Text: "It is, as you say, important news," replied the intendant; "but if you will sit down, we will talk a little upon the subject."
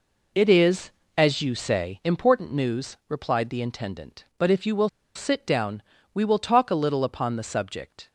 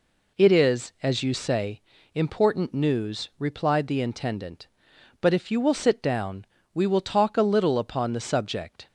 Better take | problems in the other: second | pauses between "will" and "sit"; slight; at 4.8 s; 0.26 s long

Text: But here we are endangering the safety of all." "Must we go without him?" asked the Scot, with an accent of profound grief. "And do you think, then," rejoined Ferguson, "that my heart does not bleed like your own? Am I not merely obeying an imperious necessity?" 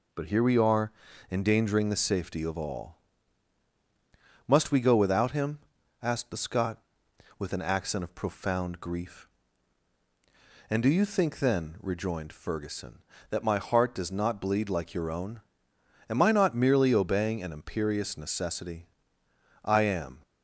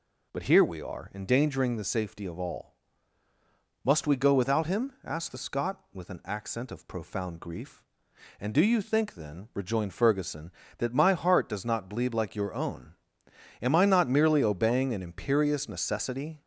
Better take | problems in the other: second | pauses between "are" and "endangering"; at 0.9 s; 0.38 s long // goes on to say "I am"; from 19.6 s on; 0.58 s long

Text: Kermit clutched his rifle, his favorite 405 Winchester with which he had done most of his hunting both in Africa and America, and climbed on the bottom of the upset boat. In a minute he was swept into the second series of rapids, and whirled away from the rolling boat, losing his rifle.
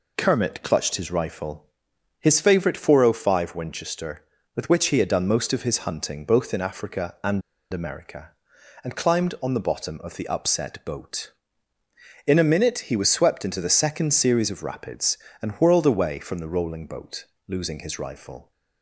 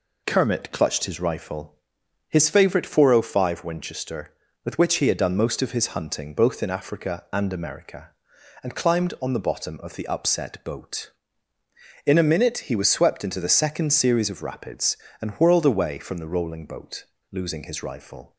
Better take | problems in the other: second | pauses between "and" and "America"; slight; at 7.4 s; 0.31 s long

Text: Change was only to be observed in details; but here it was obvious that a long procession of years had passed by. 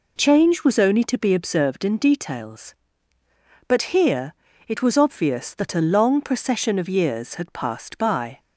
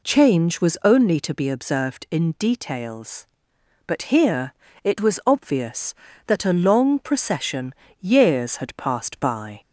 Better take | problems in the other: first | pauses between "here" and "it"; slight; at 4.5 s; 0.30 s long; slight in the first // skips "of"; at 7.8 s

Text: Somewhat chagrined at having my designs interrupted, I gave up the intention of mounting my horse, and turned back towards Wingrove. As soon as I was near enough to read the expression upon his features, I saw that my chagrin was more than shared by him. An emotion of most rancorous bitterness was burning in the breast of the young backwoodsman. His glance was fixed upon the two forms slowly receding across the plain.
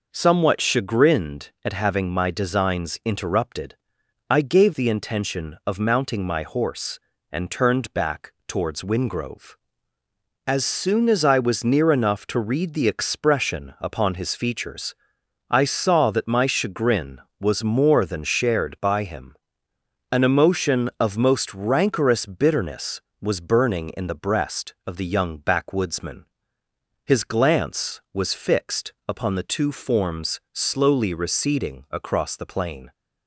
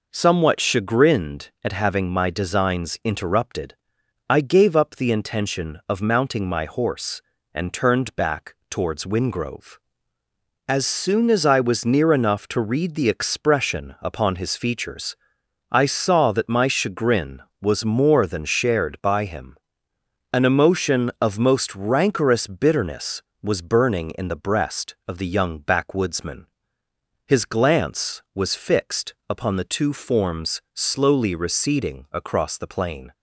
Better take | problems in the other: second | skips "up"; at 4.7 s // pauses between "back" and "towards"; slight; at 8.3 s; 0.16 s long; slight in the second

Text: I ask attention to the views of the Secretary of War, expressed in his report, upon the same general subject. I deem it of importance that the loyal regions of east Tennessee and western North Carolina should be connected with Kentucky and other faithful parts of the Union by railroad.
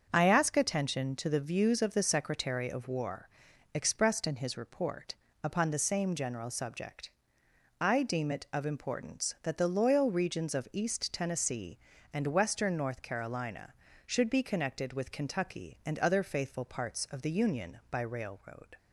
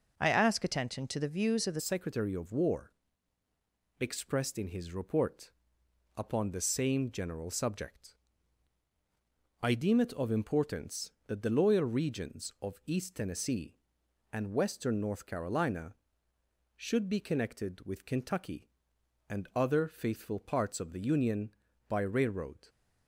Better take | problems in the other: first | starts louder than the rest; noticeable; until 1.1 s; 6 dB; also in the first // changes voice at "Secretary"; from 1.7 s on; 20.9 s long

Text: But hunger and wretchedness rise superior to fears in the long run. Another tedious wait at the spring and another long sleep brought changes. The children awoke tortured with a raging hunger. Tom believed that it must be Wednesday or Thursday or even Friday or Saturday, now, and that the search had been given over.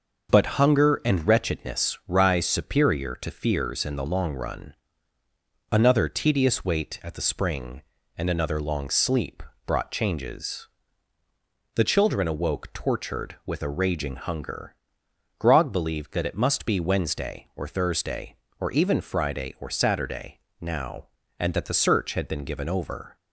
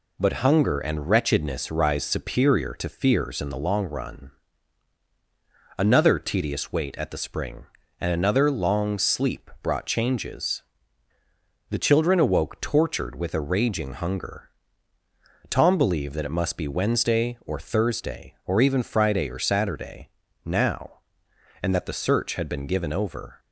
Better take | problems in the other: second | starts louder than the rest; until 1.4 s; 6 dB // pauses between "sleep" and "brought"; slight; at 9.4 s; 0.24 s long // says "Grog" for "Tom"; at 15.4 s

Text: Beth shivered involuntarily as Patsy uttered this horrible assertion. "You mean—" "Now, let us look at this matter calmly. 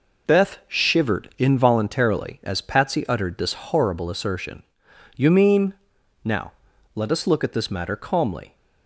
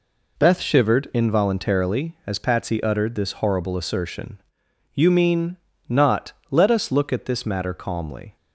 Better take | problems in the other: first | says "Not" for "Now"; at 5.8 s

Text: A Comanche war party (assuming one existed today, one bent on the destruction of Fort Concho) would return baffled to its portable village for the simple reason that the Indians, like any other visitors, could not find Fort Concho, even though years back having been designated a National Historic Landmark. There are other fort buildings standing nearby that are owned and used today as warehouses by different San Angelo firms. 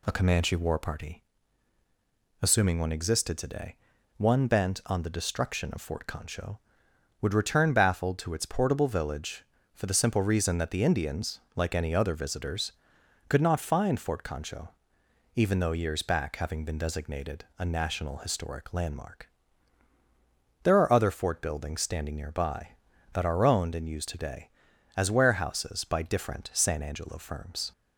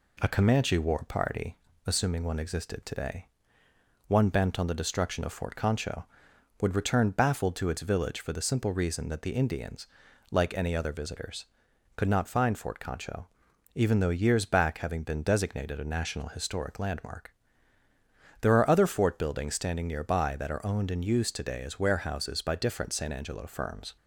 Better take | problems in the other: first | skips "portable"; at 7.8 s

